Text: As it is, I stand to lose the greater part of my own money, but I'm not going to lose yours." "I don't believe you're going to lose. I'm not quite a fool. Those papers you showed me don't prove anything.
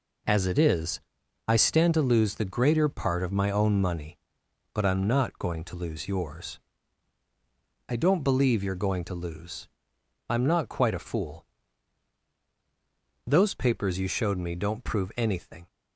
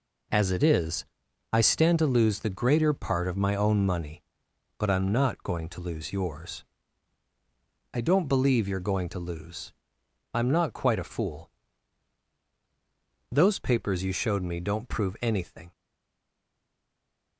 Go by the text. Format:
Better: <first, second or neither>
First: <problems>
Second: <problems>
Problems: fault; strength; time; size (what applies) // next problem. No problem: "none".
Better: first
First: none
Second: stays silent after the last word; noticeable; from 15.7 s on; 1.6 s long